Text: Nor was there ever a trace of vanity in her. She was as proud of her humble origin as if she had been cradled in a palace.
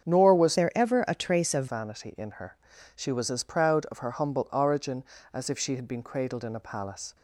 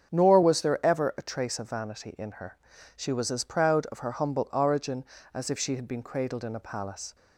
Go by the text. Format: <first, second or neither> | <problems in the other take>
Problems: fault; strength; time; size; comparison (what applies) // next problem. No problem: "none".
second | starts louder than the rest; strong; until 1.1 s; 7.5 dB; strong in the second // changes voice from "there" to "of"; from 0.5 to 1.6 s; 1.1 s long